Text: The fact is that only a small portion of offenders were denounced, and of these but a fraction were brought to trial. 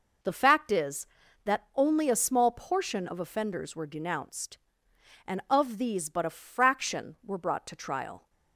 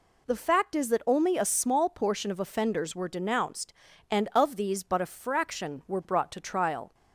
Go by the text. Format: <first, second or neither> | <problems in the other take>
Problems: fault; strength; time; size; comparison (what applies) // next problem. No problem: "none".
neither | none